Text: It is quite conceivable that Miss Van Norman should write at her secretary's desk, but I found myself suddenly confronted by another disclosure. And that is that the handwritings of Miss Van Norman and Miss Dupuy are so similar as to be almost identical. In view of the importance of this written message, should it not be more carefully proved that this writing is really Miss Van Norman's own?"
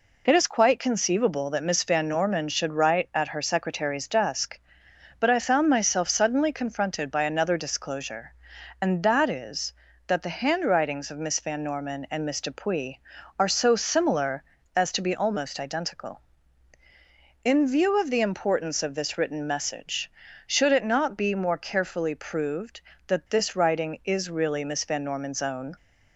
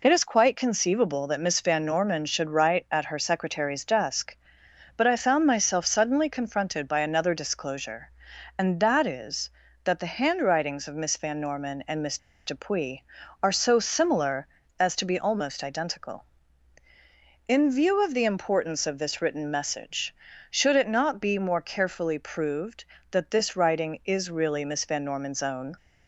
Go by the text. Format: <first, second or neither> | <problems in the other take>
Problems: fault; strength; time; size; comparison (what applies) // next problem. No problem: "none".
first | pauses between "Miss" and "Dupuy"; slight; at 12.1 s; 0.29 s long